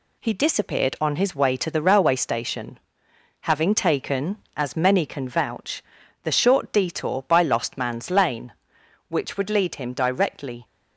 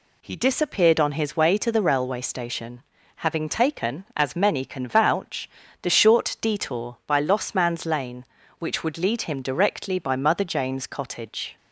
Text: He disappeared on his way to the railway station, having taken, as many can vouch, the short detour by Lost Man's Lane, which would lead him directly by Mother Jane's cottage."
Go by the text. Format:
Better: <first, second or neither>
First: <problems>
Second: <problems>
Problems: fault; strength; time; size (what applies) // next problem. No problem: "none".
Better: second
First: stops before "by Mother Jane's cottage"; at 10.6 s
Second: none